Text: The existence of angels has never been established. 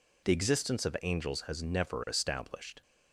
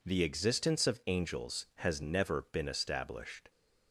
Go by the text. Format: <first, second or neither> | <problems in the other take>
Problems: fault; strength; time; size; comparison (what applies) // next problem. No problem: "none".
second | skips "been"; at 2.0 s